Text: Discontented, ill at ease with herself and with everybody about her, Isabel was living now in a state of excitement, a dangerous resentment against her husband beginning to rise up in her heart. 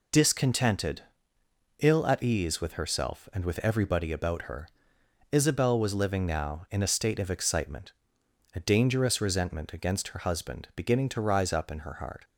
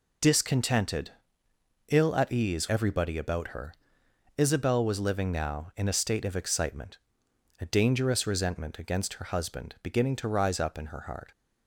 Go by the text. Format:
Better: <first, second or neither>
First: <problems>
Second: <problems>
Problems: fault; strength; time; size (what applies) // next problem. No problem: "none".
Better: first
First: none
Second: skips "with herself and with"; at 2.6 s